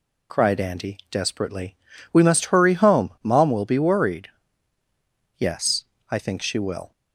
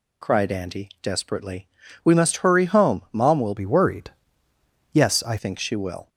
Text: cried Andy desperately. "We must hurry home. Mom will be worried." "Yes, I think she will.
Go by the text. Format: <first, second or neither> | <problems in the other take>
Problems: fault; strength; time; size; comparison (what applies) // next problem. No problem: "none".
first | changes voice from "be" to "I"; from 3.5 to 5.3 s; 1.8 s long